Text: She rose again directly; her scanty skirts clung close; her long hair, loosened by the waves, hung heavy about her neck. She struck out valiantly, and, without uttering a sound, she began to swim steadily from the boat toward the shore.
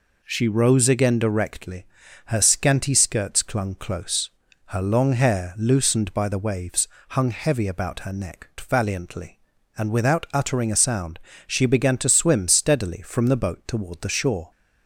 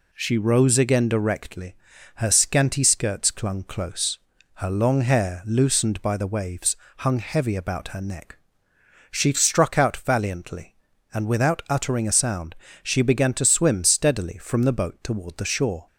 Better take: second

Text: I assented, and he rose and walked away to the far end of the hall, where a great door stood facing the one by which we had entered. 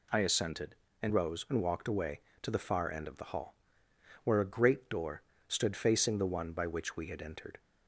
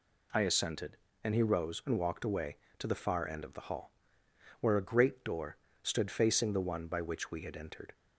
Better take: second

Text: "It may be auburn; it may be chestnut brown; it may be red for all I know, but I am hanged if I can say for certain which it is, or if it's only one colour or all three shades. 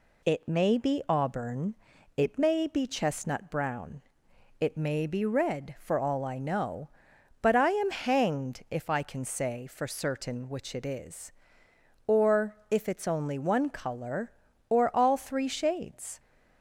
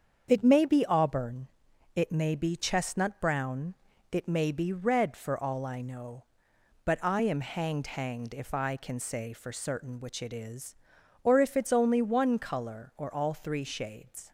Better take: first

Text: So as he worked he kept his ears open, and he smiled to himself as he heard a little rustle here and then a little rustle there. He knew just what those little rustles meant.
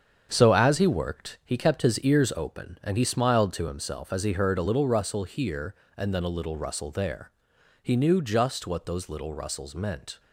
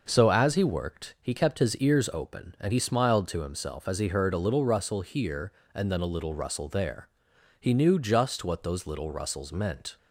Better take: second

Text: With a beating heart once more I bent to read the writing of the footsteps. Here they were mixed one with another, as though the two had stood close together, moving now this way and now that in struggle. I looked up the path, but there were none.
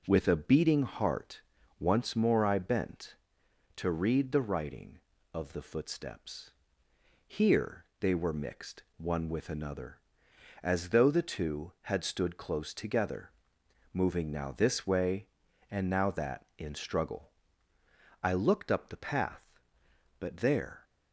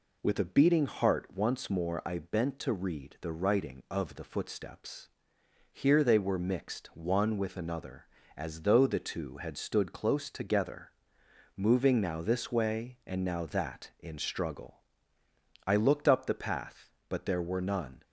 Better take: second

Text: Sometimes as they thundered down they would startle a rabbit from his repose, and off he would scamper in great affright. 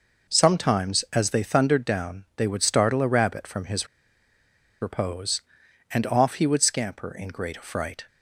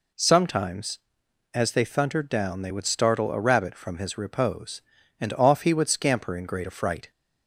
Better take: second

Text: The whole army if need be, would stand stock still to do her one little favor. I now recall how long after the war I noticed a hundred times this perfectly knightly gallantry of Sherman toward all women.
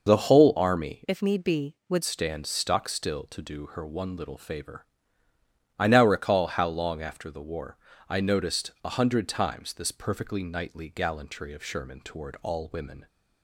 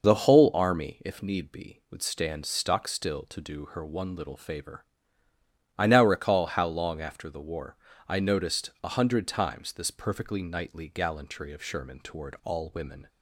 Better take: second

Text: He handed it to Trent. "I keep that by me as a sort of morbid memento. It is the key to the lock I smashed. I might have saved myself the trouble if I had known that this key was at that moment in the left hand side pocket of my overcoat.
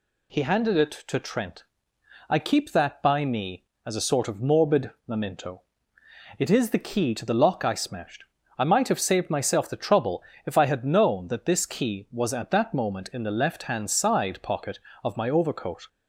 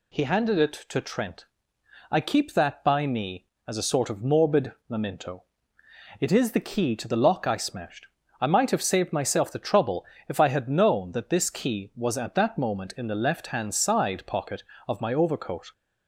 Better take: neither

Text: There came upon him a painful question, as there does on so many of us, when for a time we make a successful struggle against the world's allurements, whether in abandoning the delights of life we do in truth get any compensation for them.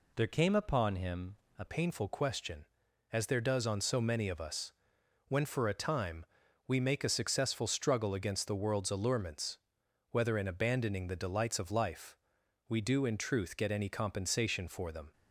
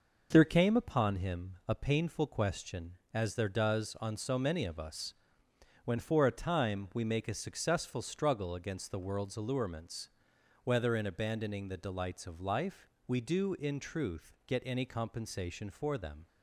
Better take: second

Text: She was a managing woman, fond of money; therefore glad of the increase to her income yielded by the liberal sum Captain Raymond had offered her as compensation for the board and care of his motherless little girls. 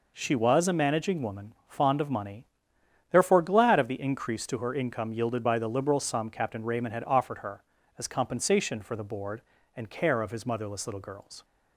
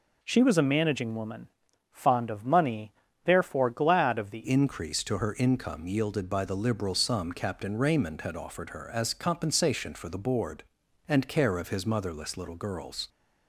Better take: first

